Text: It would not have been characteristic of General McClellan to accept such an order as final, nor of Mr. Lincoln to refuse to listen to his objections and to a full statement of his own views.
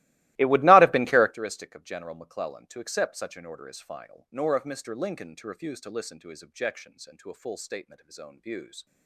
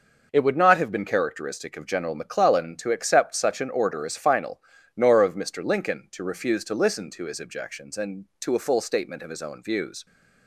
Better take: second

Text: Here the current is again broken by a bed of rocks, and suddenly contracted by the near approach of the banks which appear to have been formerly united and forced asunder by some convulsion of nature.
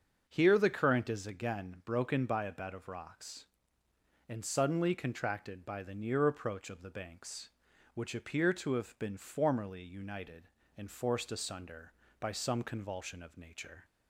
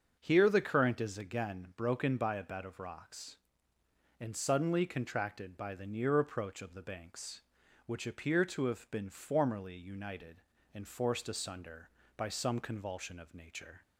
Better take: neither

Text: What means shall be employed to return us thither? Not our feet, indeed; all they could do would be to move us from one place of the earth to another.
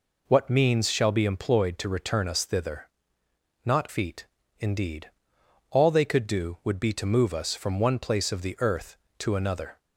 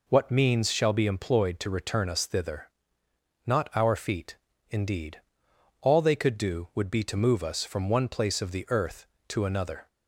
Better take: second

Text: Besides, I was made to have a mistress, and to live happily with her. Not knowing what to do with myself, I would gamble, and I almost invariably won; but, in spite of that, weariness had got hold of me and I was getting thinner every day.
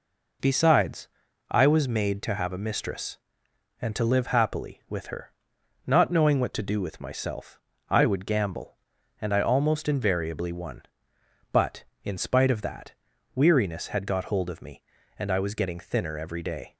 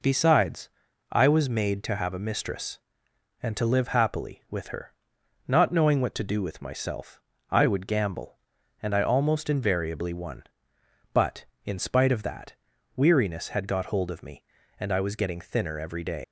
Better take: first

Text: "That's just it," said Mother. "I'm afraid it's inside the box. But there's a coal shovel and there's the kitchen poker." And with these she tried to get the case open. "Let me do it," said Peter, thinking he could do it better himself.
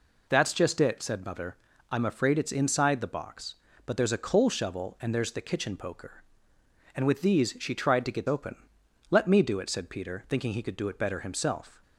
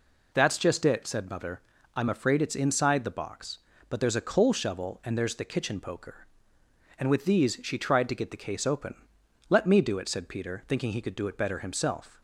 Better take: second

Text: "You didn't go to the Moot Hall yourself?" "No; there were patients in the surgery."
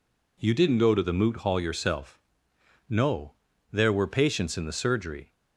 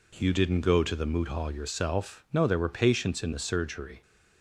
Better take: neither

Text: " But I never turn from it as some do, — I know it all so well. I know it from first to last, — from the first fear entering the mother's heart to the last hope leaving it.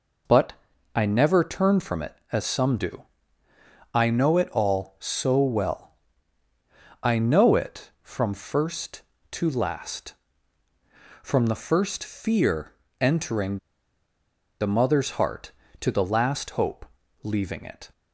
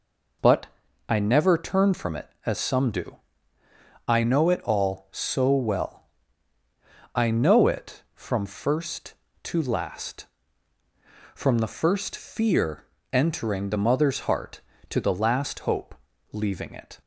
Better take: second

